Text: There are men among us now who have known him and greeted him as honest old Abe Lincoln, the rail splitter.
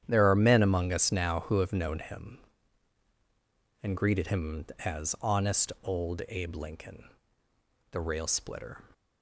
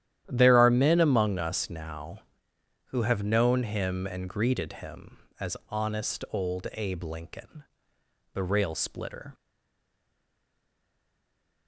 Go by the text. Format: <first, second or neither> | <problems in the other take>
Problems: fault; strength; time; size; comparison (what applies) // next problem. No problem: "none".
first | starts louder than the rest; strong; until 1.2 s; 11.5 dB; strong in the first // stays silent after the last word; from 9.3 s on; 2.3 s long